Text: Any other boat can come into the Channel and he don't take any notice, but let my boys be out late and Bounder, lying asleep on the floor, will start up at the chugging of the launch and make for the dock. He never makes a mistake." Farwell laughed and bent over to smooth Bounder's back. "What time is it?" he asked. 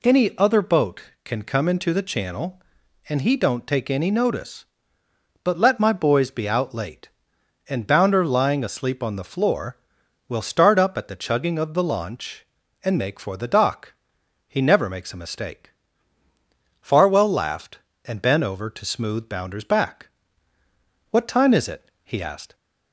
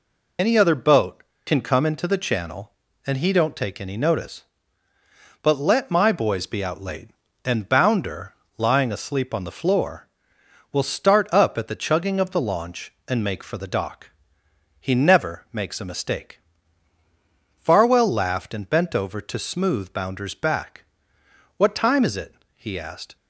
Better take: first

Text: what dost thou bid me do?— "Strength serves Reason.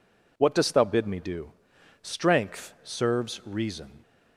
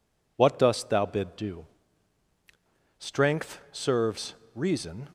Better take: first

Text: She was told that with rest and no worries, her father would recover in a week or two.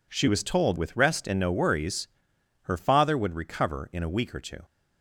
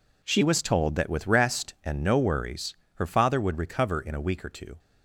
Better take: second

